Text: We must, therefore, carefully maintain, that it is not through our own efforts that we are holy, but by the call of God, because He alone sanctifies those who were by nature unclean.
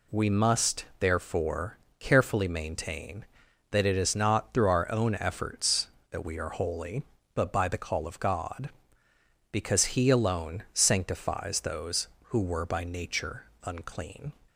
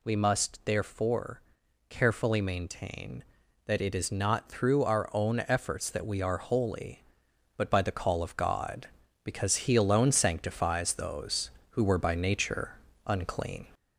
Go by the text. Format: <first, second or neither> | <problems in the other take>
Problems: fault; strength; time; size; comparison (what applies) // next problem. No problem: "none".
first | gets louder; slight; throughout; 2.5 dB // pauses between "nature" and "unclean"; slight; at 12.7 s; 0.34 s long; slight in the first